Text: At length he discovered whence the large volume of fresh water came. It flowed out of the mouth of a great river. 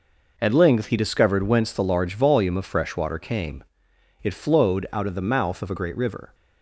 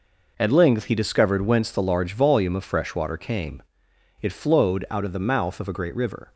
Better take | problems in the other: neither | none

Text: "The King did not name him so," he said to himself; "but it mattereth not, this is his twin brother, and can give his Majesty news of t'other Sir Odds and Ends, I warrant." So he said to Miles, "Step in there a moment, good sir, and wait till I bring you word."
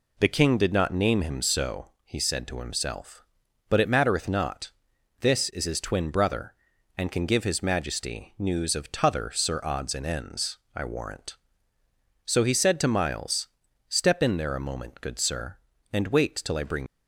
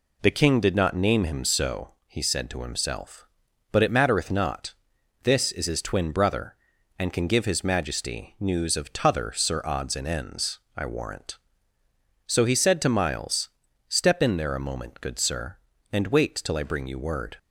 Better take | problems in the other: second | stops before "you word"; at 16.8 s

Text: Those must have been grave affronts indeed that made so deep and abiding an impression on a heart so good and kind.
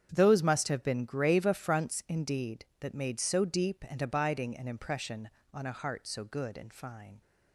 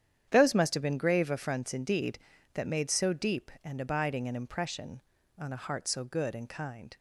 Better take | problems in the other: second | starts louder than the rest; strong; until 1.1 s; 8.5 dB; strong in the second // says "fine" for "kind"; at 6.7 s

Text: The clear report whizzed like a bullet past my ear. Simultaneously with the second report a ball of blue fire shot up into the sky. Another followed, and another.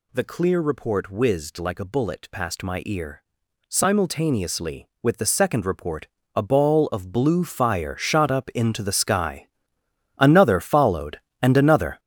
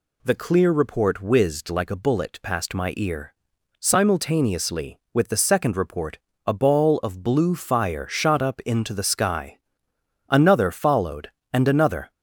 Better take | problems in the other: second | gets louder; strong; throughout; 10 dB // pauses between "report" and "a"; slight; at 6.0 s; 0.28 s long; slight in the second

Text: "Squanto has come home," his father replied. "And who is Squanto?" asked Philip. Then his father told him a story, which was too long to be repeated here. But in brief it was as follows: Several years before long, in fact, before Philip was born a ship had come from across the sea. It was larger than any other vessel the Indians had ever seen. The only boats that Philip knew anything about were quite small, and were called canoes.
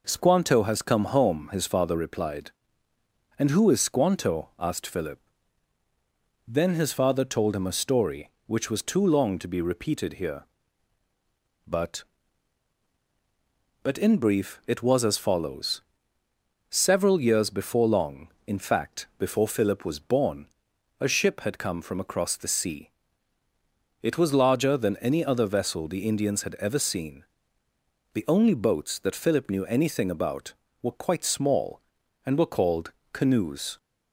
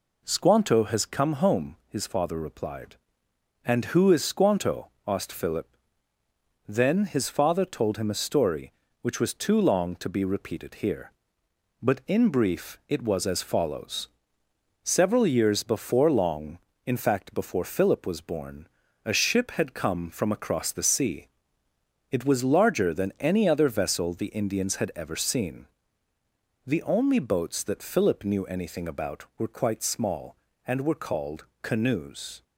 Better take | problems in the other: second | says "But" twice; at 13.8 s // pauses between "born" and "a"; noticeable; at 20.4 s; 0.52 s long; also in the second // pauses between "called" and "canoes"; slight; at 32.9 s; 0.18 s long; slight in the second

